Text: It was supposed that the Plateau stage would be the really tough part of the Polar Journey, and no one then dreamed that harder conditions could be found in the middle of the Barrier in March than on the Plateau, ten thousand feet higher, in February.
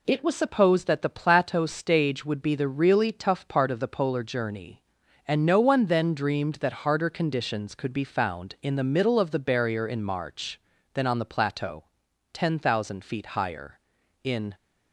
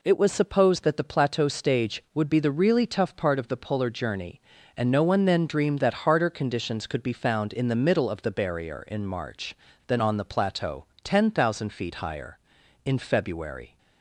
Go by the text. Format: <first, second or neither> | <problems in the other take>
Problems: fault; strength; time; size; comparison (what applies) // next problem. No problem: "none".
second | stops before "February"; at 14.5 s